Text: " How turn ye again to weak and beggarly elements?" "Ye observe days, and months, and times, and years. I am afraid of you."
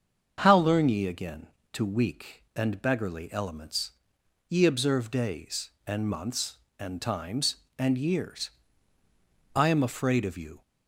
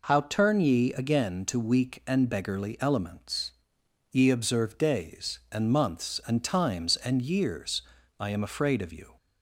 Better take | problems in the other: second | starts louder than the rest; until 1.3 s; 7 dB // says "learn" for "turn"; at 0.5 s

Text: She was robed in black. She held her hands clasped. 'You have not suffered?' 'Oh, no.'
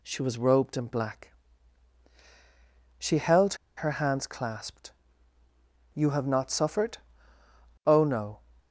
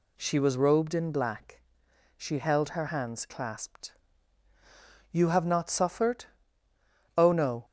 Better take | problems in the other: second | pauses between "held" and "her"; slight; at 3.5 s; 0.22 s long

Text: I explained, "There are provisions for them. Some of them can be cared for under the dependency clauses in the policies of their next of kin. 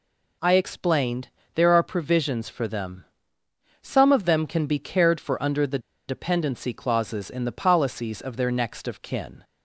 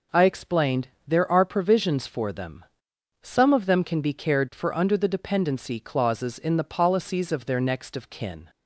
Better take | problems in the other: second | pauses between "the" and "dependency"; slight; at 5.7 s; 0.29 s long

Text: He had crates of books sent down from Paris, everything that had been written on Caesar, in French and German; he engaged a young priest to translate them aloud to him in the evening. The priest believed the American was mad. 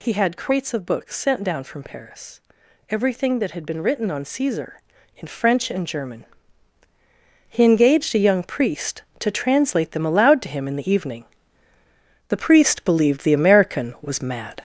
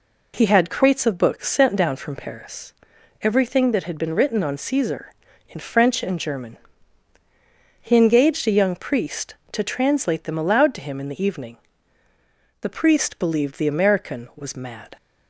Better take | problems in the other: second | gets louder; noticeable; throughout; 5.5 dB

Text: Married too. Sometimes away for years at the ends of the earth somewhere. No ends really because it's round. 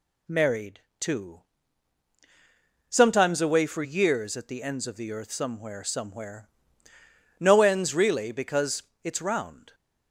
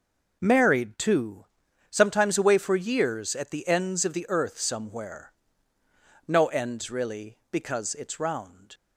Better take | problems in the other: second | pauses between "Married" and "too"; slight; at 0.8 s; 0.18 s long // says "somewhere" twice; at 5.8 s // pauses between "because" and "it's"; slight; at 8.8 s; 0.20 s long

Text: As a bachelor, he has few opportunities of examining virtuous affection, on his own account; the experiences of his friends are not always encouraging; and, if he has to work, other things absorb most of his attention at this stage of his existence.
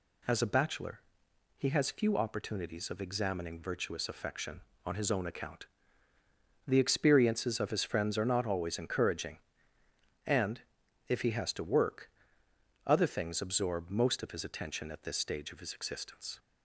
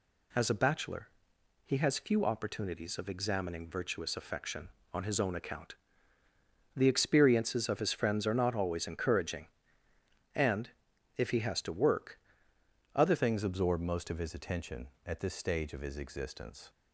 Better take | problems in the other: first | changes voice at "things"; from 13.1 s on; 3.5 s long

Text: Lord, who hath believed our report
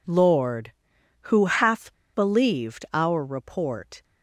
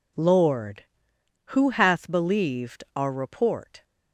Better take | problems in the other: second | pauses between "hath" and "believed"; slight; at 1.9 s; 0.20 s long

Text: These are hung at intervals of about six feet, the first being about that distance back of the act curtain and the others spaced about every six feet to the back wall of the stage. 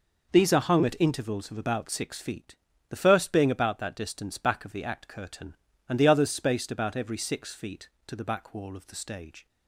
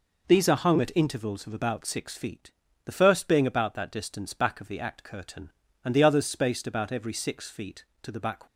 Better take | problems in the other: first | stops before "wall of the stage"; at 8.4 s

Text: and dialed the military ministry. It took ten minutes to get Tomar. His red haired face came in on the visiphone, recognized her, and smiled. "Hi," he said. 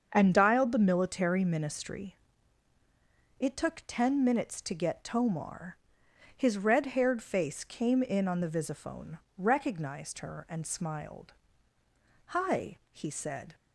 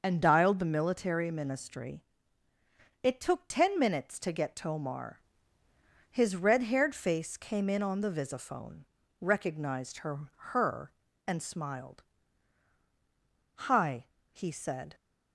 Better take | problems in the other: first | starts louder than the rest; noticeable; until 1.0 s; 6 dB; also in the first // says "her" twice; at 10.3 s

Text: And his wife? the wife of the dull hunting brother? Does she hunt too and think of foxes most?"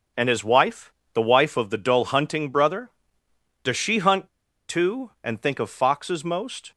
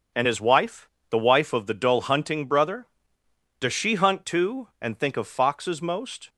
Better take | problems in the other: second | starts louder than the rest; strong; until 1.4 s; 7 dB; strong in the second // pauses between "hunt" and "too"; at 4.2 s; 0.39 s long

